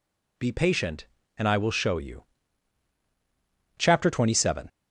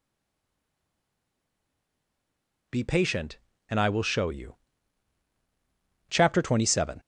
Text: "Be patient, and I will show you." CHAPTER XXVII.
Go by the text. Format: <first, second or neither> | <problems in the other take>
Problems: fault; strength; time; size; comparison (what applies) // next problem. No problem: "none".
first | stays silent before the first word; strong; until 2.6 s; 2.6 s long